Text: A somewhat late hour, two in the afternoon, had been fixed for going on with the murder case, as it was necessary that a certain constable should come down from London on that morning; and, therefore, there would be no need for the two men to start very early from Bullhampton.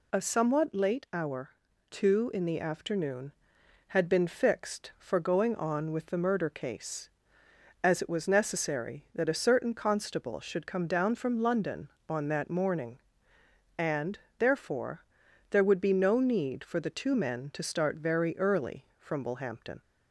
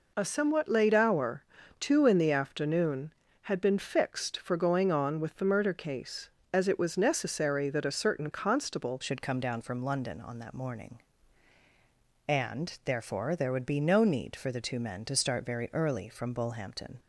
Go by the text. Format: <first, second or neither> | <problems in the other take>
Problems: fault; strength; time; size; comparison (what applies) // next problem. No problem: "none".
first | changes voice at "should"; from 9.0 s on; 7.9 s long